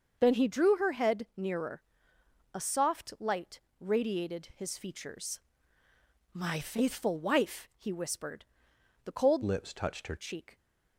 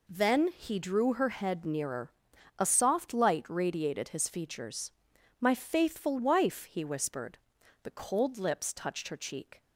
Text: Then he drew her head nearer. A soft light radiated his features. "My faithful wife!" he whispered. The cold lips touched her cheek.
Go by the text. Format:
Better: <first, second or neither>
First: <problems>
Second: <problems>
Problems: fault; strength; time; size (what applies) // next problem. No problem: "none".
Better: second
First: starts louder than the rest; noticeable; until 1.2 s; 6 dB // pauses between "light" and "radiated"; slight; at 3.5 s; 0.20 s long // changes voice from "lips" to "her"; from 9.4 to 10.1 s; 0.7 s long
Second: none